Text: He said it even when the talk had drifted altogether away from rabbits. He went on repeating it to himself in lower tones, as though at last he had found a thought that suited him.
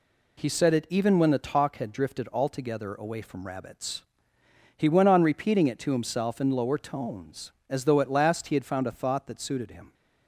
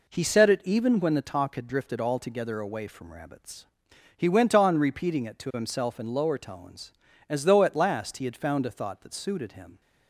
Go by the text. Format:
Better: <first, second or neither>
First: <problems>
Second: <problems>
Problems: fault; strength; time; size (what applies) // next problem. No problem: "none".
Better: neither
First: none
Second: none